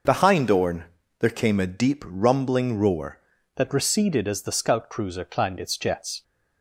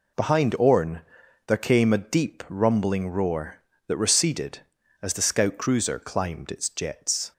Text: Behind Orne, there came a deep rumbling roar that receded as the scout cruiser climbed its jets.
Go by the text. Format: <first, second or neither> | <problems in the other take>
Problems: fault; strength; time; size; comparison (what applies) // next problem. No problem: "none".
second | changes voice at "that"; from 3.5 s on; 2.7 s long